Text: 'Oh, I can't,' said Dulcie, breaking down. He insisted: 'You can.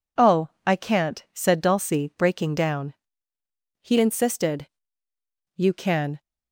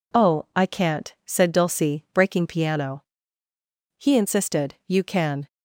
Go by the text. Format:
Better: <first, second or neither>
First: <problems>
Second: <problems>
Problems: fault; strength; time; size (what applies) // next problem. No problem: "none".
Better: first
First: none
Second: says "piano" for "down"; at 2.4 s